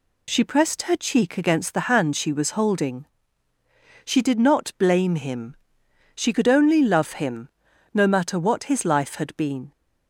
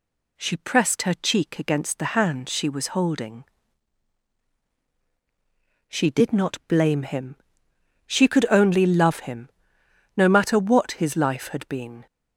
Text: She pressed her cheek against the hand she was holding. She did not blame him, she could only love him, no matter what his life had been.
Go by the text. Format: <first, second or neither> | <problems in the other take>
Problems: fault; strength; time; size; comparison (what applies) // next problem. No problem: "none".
neither | none